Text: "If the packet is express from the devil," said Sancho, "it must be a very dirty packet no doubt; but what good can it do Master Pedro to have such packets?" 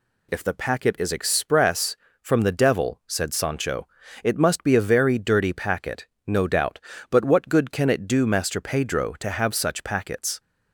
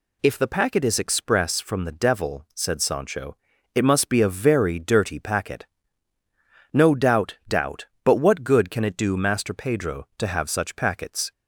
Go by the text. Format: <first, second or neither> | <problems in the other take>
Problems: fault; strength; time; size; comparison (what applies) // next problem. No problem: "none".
first | pauses between "packet" and "no"; at 5.6 s; 1.0 s long; slight in the first // says "doubt" twice; at 7.4 s